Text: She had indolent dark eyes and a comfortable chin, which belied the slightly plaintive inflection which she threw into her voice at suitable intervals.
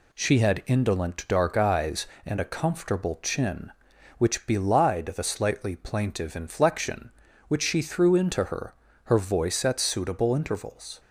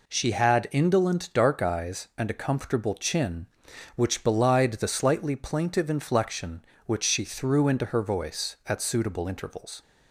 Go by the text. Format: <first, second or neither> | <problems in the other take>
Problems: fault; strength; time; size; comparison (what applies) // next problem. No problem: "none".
second | says "her" twice; at 9.0 s